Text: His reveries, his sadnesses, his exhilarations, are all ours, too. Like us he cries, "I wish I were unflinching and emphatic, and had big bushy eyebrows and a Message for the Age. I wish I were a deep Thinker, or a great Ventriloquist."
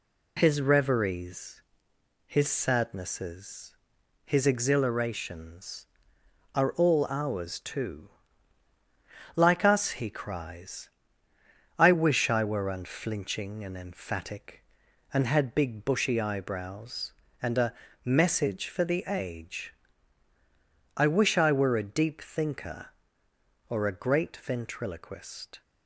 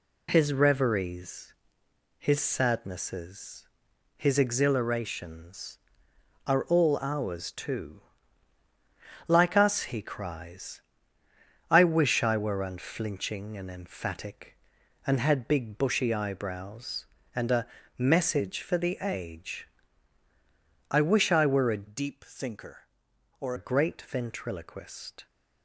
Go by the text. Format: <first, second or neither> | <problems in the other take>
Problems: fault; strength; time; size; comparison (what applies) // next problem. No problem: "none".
first | pauses between "a" and "Message"; slight; at 17.6 s; 0.32 s long; slight in the first // changes voice from "deep" to "or"; from 21.8 to 23.5 s; 1.7 s long